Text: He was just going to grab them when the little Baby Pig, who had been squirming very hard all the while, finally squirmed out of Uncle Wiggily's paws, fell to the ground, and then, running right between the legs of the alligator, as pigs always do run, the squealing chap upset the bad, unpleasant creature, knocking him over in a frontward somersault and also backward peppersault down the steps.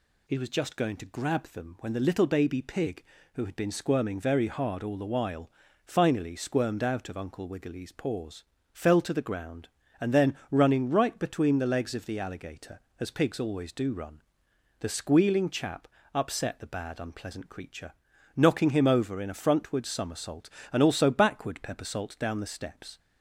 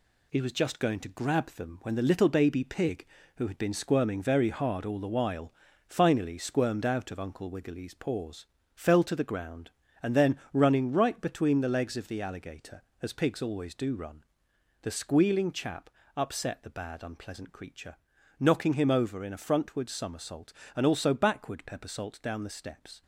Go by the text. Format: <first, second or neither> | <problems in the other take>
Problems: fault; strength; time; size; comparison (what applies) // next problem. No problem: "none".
first | gets quieter; noticeable; throughout; 5.5 dB // pauses between "chap" and "upset"; slight; at 15.8 s; 0.26 s long; slight in the first